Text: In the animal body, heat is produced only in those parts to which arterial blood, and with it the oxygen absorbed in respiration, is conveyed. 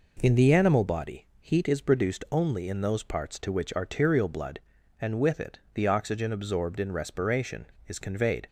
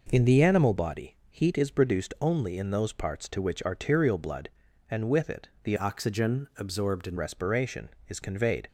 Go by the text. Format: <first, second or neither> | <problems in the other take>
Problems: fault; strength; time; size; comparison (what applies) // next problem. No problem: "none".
first | changes voice from "oxygen" to "in"; from 5.7 to 7.1 s; 1.4 s long